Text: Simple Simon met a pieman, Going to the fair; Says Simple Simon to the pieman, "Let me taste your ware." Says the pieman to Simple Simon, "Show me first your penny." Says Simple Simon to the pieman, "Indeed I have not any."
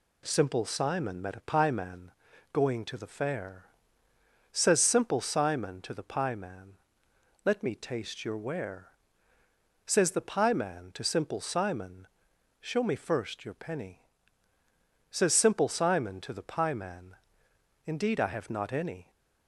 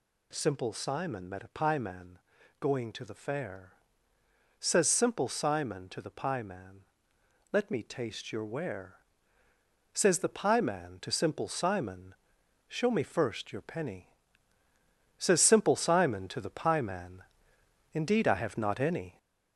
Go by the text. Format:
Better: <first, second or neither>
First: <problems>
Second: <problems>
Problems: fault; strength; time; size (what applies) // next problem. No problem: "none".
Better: first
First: none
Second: gets louder; throughout; 3.5 dB